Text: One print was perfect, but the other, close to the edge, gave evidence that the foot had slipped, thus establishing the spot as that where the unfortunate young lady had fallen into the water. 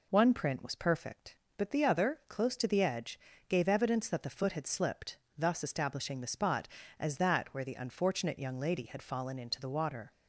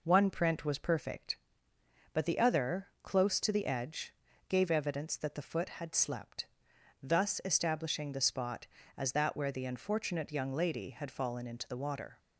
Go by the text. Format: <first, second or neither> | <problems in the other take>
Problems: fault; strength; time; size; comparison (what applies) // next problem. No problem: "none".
first | says "slept" for "slipped"; at 5.9 s